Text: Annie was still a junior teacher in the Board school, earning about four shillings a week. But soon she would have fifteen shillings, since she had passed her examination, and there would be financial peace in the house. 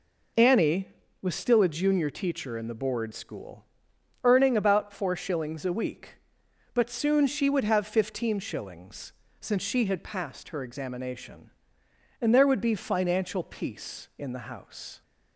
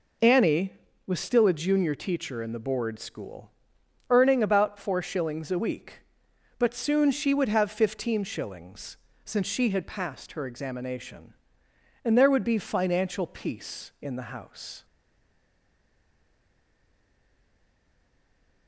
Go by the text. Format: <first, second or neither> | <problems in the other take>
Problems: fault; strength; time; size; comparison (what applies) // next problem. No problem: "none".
first | stays silent after the last word; strong; from 14.8 s on; 3.8 s long